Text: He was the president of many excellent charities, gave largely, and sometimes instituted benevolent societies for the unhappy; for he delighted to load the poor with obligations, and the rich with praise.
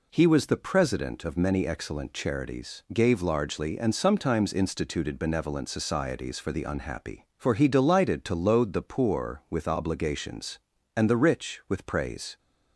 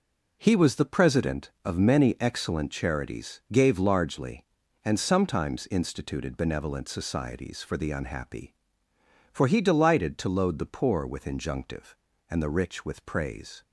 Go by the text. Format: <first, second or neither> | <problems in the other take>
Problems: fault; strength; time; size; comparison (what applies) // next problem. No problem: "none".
first | says "injunctive" for "obligations"; at 11.2 s